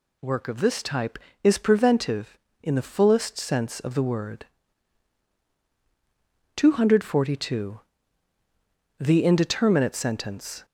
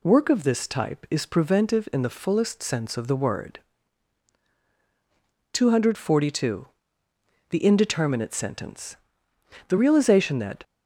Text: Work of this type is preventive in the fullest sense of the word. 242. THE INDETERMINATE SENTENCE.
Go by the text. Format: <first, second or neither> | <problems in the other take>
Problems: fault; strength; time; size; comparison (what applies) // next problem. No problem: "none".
first | goes on to say "The realization that"; noticeable; from 9.6 s on; 0.95 s long